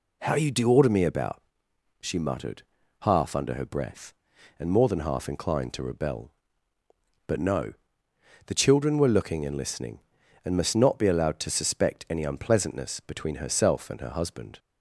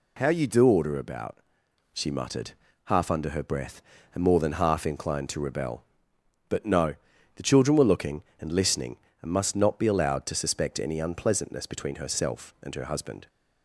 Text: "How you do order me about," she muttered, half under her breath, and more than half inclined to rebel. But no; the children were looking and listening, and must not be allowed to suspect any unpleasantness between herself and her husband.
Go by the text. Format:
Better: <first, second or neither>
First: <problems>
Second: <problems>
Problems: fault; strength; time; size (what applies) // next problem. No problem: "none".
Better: first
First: none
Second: skips "me"; at 0.9 s